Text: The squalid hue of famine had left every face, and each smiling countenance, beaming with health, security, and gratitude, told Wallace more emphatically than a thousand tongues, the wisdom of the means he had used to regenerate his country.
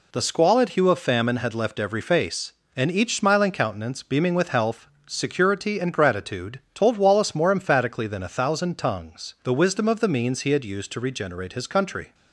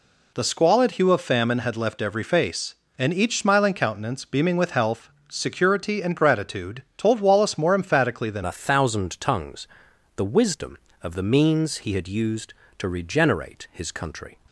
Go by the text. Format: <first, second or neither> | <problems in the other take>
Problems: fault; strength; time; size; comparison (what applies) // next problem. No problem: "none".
first | changes voice at "a"; from 8.4 s on; 5.9 s long